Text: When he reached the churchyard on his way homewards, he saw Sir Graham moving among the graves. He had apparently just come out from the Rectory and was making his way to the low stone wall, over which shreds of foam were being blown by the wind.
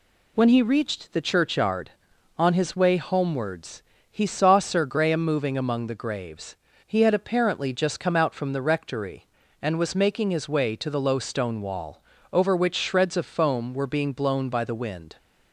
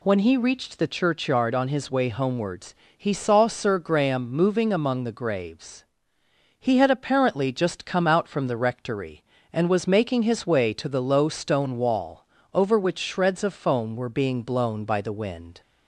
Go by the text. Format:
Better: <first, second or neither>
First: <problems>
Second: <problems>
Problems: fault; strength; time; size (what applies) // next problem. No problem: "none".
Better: neither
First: none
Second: none